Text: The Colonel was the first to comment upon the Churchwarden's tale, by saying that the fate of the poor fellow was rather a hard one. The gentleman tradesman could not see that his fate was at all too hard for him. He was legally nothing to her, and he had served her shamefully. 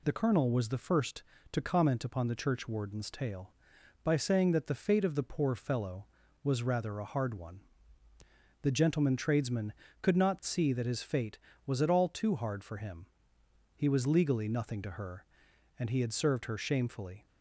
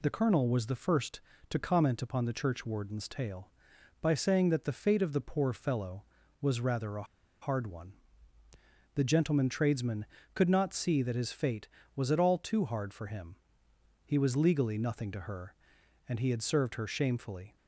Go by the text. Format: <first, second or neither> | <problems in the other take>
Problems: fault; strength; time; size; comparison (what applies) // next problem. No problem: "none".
first | pauses between "a" and "hard"; at 7.0 s; 0.37 s long